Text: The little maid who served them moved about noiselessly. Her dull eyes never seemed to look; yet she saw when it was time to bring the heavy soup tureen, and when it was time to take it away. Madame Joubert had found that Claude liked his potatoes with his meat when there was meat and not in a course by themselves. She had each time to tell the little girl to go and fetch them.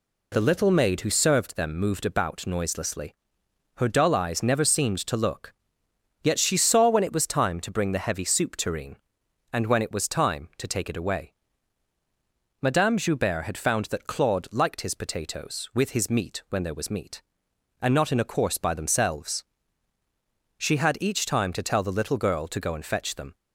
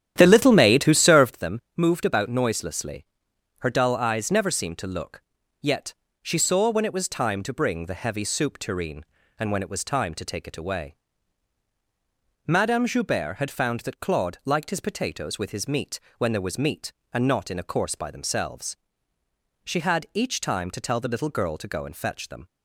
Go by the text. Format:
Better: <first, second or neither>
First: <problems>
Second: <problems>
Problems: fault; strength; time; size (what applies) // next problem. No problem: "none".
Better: first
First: none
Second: starts louder than the rest; strong; until 1.4 s; 10.5 dB // pauses between "them" and "moved"; slight; at 1.5 s; 0.18 s long // pauses between "yet" and "she"; slight; at 5.9 s; 0.30 s long // pauses between "meat" and "when"; slight; at 15.9 s; 0.18 s long